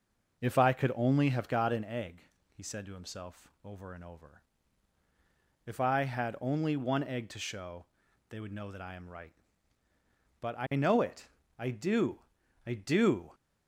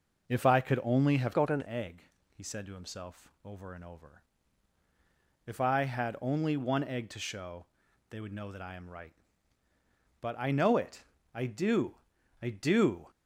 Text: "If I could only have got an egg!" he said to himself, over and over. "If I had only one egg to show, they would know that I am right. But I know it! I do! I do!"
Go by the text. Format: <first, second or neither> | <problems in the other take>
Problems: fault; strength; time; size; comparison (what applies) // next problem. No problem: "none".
first | changes voice from "got" to "an"; from 1.3 to 1.6 s; 0.3 s long